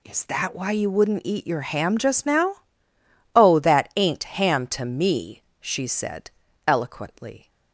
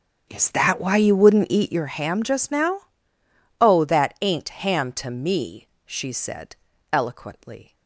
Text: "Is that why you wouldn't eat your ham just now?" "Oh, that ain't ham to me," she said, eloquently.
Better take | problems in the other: first | starts louder than the rest; strong; until 1.9 s; 8.5 dB

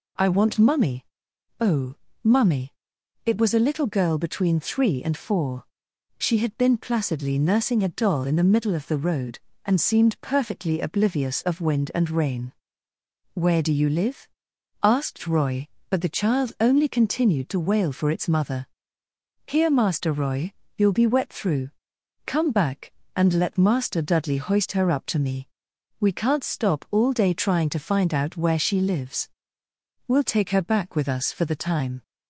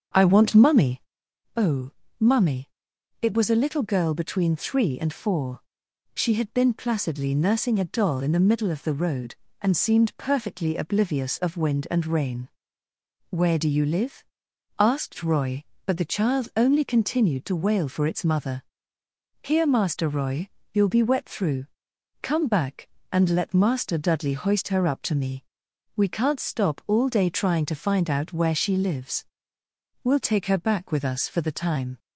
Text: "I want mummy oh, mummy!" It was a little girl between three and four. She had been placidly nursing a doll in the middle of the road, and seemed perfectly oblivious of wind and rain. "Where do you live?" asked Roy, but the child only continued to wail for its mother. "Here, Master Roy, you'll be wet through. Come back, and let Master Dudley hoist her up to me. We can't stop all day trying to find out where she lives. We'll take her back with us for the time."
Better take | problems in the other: first | starts louder than the rest; until 1.1 s; 7 dB // pauses between "mummy" and "oh"; noticeable; at 1.0 s; 0.56 s long; noticeable in the first

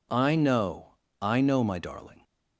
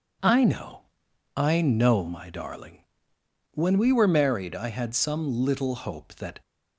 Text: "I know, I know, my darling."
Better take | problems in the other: first | goes on to say "When we were married I had some little hope that"; strong; from 3.5 s on; 2.8 s long

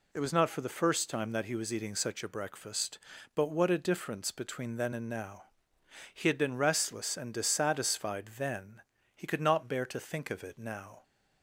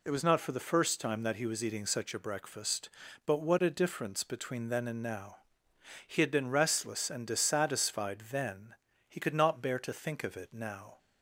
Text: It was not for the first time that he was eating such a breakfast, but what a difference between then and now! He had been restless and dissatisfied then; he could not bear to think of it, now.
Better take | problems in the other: neither | none

